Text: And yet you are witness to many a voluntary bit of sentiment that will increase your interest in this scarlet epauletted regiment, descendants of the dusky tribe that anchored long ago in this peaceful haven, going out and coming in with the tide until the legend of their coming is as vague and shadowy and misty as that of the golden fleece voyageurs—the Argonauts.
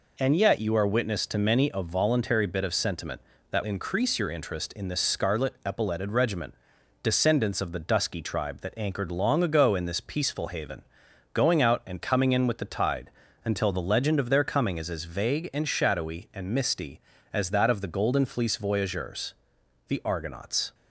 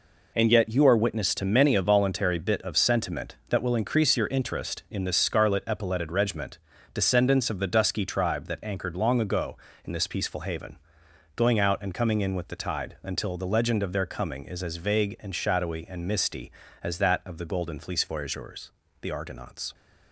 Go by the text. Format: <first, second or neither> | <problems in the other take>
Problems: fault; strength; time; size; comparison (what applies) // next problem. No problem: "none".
second | skips "will"; at 3.6 s // pauses between "tide" and "until"; slight; at 13.0 s; 0.34 s long